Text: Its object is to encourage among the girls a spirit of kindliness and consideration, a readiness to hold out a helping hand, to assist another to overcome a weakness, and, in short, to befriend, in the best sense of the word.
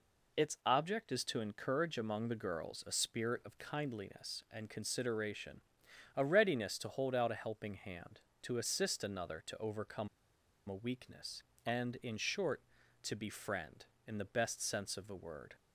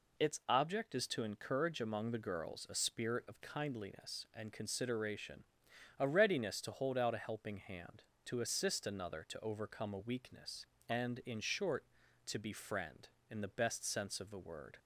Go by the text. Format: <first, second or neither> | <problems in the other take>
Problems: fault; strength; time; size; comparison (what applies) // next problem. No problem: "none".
second | pauses between "overcome" and "a"; noticeable; at 10.0 s; 0.59 s long